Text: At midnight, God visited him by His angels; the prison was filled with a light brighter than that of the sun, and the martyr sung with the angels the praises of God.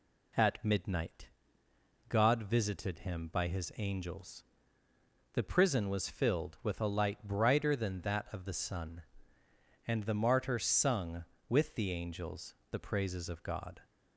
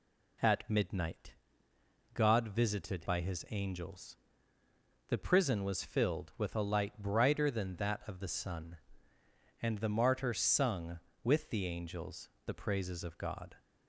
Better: first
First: pauses between "angels" and "the"; slight; at 12.5 s; 0.16 s long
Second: skips "him"; at 3.0 s // pauses between "angels" and "the"; slight; at 12.2 s; 0.16 s long

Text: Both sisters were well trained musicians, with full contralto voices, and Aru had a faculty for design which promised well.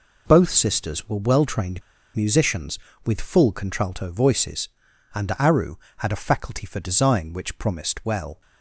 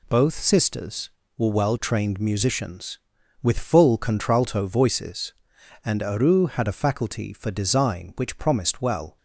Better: second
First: pauses between "trained" and "musicians"; slight; at 1.8 s; 0.34 s long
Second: none

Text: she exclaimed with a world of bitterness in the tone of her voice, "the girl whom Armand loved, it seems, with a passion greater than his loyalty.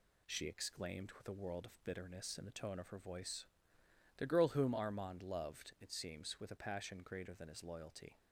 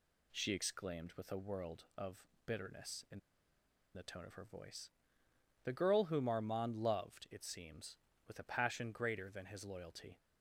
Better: first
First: none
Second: pauses between "of" and "bitterness"; slight; at 2.2 s; 0.20 s long // pauses between "in" and "the"; noticeable; at 3.1 s; 0.75 s long

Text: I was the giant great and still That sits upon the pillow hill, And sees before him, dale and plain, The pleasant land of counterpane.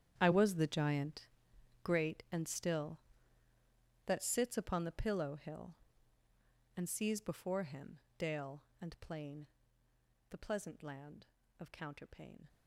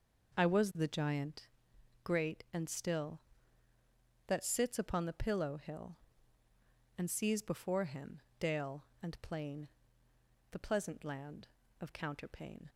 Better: second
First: gets quieter; strong; throughout; 16 dB // pauses between "giant" and "great"; noticeable; at 1.2 s; 0.56 s long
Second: pauses between "giant" and "great"; noticeable; at 1.4 s; 0.56 s long

